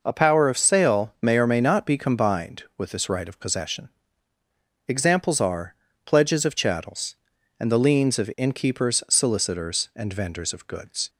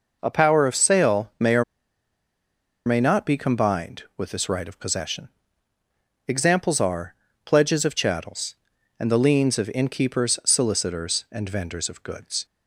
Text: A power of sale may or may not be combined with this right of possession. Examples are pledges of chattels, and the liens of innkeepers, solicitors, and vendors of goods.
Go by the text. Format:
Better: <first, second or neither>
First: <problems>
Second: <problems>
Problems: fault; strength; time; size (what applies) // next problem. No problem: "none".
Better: first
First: pauses between "are" and "pledges"; slight; at 5.7 s; 0.30 s long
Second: pauses between "or" and "may"; at 1.6 s; 1.2 s long // pauses between "are" and "pledges"; slight; at 7.1 s; 0.30 s long